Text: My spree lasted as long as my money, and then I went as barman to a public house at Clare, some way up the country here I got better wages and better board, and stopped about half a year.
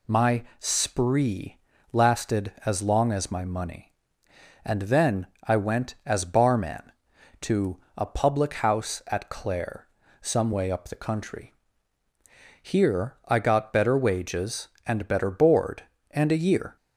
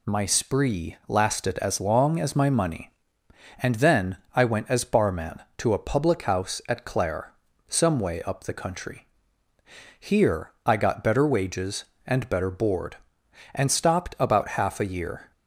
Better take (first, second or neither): second